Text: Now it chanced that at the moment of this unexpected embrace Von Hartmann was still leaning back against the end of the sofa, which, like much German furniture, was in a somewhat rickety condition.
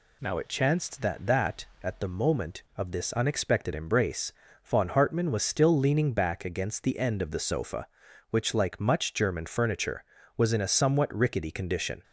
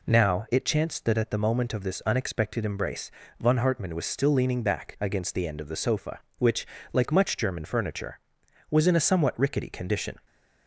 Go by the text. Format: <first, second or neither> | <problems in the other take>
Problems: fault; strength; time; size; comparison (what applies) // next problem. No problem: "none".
second | says "that" twice; at 1.2 s // pauses between "embrace" and "Von"; slight; at 4.3 s; 0.32 s long; slight in the second